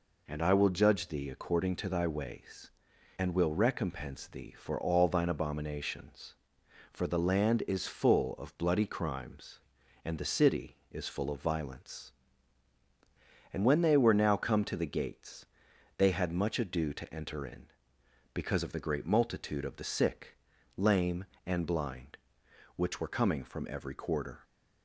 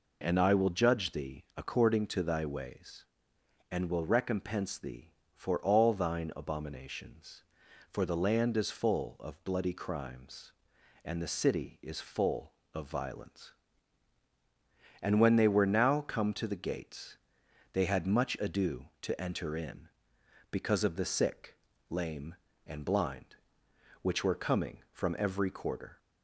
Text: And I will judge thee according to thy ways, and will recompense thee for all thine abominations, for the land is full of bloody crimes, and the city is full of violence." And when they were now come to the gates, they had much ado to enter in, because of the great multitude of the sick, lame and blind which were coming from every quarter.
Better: first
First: none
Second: skips "great multitude of the"; at 21.0 s

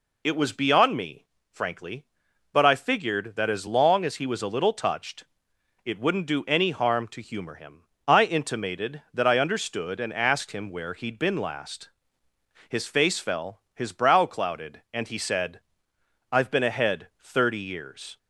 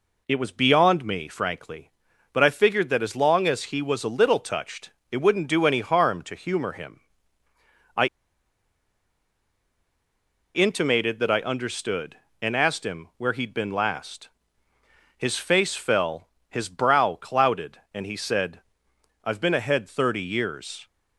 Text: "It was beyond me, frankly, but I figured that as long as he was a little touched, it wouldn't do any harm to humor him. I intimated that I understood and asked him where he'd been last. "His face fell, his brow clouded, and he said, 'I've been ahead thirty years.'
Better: first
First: none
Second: pauses between "I" and "intimated"; strong; at 8.0 s; 2.4 s long

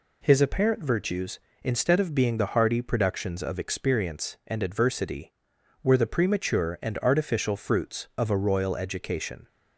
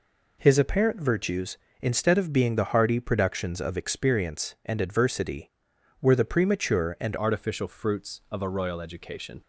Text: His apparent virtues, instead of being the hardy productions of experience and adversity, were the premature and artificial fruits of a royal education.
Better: first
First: none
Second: changes voice at "artificial"; from 7.1 s on; 2.3 s long

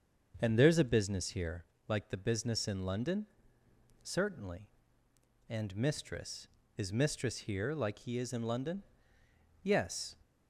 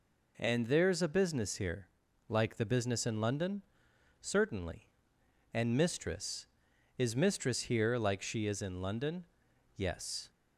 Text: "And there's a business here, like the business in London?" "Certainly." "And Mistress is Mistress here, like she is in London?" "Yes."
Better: second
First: starts louder than the rest; until 1.4 s; 6.5 dB // says "he" for "she"; at 7.9 s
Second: none

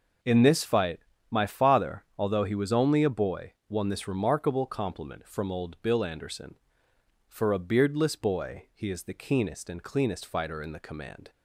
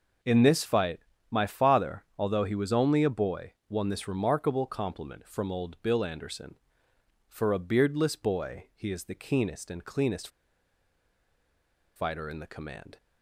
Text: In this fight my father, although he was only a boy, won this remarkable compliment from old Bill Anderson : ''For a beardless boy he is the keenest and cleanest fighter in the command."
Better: first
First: pauses between "fight" and "my"; slight; at 0.9 s; 0.32 s long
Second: pauses between "fight" and "my"; slight; at 0.9 s; 0.32 s long // pauses between "cleanest" and "fighter"; strong; at 10.2 s; 1.6 s long

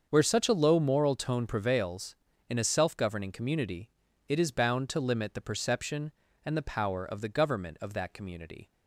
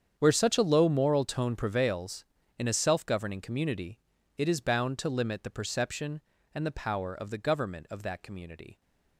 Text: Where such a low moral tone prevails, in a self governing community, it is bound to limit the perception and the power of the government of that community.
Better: first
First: starts louder than the rest; until 1.0 s; 7 dB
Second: gets quieter; strong; throughout; 16.5 dB // starts louder than the rest; strong; until 1.1 s; 8 dB

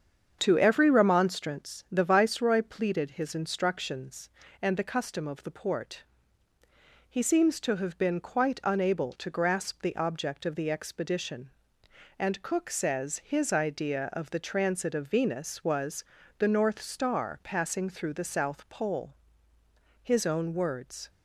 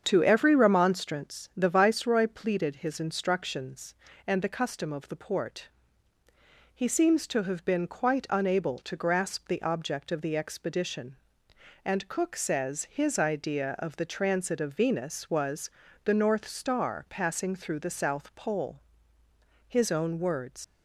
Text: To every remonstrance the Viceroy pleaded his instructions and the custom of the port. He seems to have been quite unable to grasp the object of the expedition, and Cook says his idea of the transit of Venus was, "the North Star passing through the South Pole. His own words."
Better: first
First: starts louder than the rest; strong; until 1.4 s; 7.5 dB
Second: starts louder than the rest; strong; until 1.0 s; 7.5 dB // leaves "words" unfinished; at 20.6 s; 105 ms

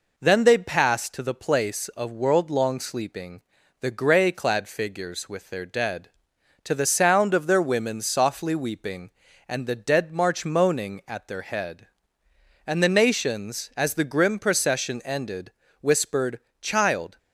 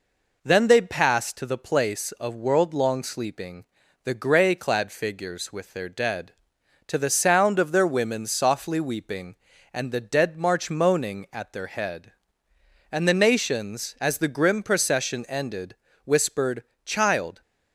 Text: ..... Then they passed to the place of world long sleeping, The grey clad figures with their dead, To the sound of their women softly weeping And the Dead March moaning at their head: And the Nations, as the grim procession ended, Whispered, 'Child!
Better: neither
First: none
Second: none

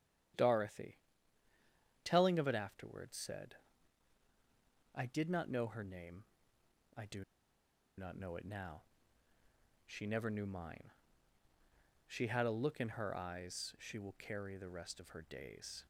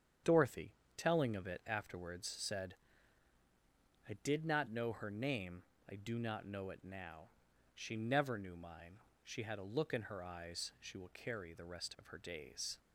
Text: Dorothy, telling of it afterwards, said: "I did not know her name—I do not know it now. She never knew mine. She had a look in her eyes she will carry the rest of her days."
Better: second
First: starts louder than the rest; strong; until 2.4 s; 10.5 dB // pauses between "do" and "not"; noticeable; at 7.2 s; 0.74 s long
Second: starts louder than the rest; strong; until 1.5 s; 8.5 dB

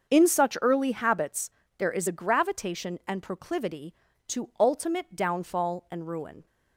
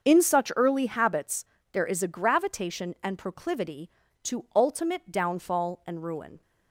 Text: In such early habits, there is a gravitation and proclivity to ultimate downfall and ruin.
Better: neither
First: starts louder than the rest; until 1.1 s; 6.5 dB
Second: starts louder than the rest; until 1.0 s; 6.5 dB

